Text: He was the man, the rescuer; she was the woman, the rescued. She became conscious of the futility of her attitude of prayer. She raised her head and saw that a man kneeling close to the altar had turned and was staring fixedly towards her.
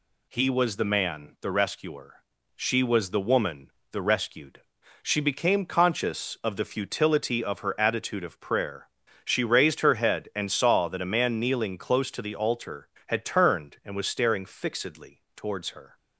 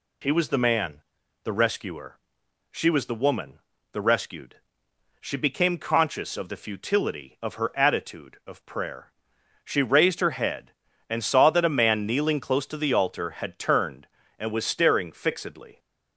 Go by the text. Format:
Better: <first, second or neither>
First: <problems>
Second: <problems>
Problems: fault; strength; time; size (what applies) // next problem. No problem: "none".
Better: first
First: none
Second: stops before "towards her"; at 15.7 s